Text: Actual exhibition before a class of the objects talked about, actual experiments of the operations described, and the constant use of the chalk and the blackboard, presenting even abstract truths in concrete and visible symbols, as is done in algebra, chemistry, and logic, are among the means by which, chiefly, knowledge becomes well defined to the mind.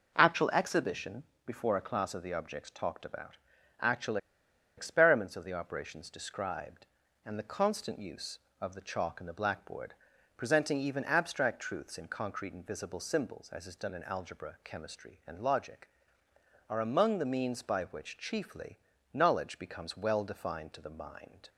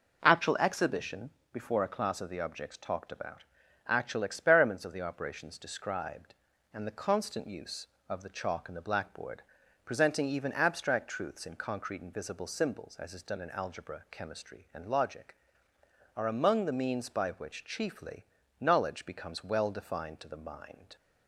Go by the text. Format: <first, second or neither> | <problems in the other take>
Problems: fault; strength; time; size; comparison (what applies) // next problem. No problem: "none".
second | pauses between "exhibition" and "before"; slight; at 1.2 s; 0.22 s long; slight in the second // pauses between "actual" and "experiments"; noticeable; at 4.1 s; 0.60 s long